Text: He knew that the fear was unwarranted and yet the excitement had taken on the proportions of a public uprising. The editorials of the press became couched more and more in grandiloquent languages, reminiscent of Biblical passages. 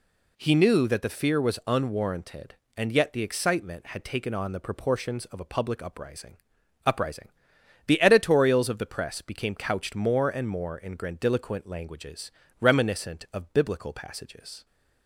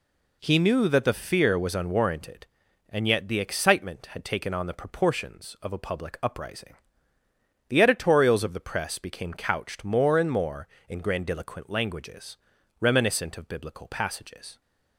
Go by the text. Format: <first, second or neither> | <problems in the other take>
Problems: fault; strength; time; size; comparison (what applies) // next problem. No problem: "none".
second | says "uprising" twice; at 6.8 s